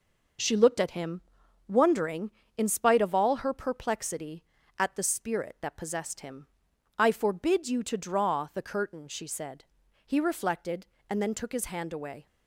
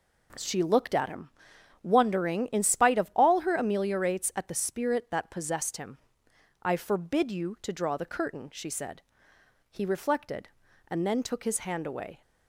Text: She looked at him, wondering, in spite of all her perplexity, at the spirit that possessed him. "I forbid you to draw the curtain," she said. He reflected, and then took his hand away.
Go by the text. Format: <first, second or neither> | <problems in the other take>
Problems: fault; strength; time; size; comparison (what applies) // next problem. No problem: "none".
first | says "ameliorates" for "perplexity"; at 3.5 s